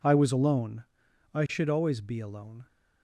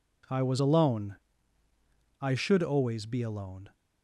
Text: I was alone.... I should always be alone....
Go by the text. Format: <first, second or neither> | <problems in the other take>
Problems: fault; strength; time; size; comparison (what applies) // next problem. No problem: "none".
neither | none